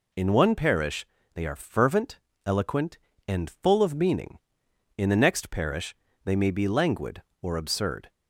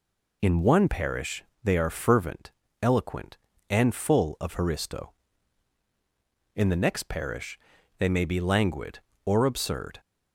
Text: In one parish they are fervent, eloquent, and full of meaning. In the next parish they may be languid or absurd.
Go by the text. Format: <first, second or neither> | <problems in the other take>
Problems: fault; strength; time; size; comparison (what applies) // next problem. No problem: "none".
first | pauses between "parish" and "they"; slight; at 1.4 s; 0.18 s long; slight in the first // says "haristo" for "meaning"; at 4.5 s // pauses between "parish" and "they"; at 7.5 s; 0.40 s long; slight in the first